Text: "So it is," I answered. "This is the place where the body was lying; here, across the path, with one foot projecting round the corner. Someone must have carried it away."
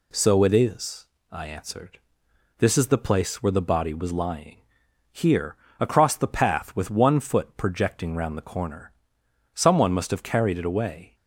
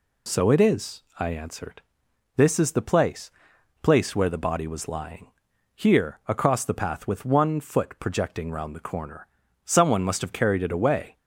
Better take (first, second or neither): first